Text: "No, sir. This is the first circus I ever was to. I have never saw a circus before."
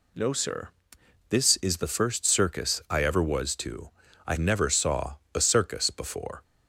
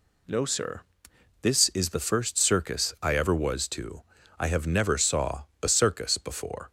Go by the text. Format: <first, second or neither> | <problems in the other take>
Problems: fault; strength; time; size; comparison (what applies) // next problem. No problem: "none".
second | skips "have"; at 4.3 s // pauses between "saw" and "a"; slight; at 5.1 s; 0.16 s long; slight in the second